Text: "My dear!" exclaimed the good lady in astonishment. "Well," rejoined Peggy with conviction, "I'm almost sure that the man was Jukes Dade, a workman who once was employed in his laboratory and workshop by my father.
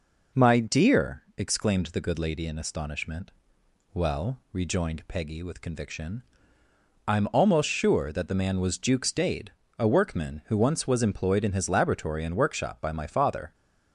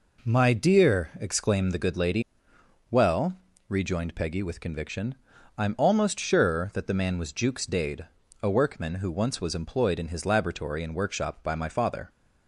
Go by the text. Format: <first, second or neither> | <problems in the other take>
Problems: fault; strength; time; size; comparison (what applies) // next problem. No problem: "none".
first | skips "in astonishment"; at 2.5 s